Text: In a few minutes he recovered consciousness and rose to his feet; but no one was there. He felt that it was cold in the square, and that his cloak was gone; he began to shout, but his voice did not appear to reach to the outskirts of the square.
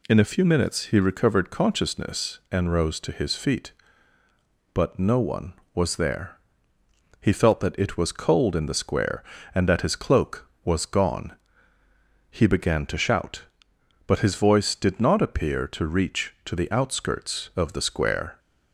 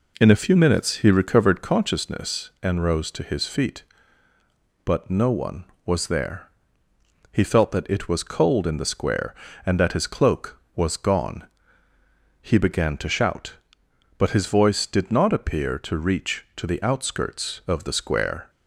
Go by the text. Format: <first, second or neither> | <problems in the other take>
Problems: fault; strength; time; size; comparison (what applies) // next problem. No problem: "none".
first | starts louder than the rest; noticeable; until 1.8 s; 4 dB